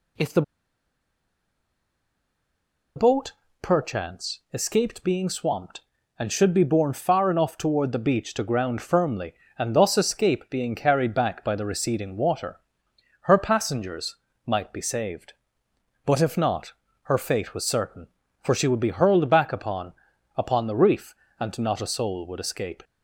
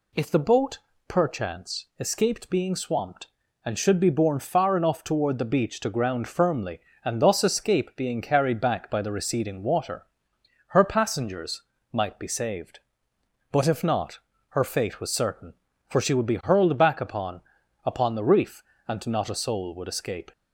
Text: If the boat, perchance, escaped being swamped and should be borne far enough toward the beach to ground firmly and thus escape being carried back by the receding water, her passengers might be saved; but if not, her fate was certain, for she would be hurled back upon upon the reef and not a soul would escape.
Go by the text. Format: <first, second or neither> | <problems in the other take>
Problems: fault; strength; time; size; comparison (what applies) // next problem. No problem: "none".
second | pauses between "the" and "boat"; strong; at 0.4 s; 2.5 s long // pauses between "passengers" and "might"; slight; at 14.1 s; 0.30 s long; slight in the second // pauses between "upon" and "upon"; at 19.9 s; 0.42 s long; also in the second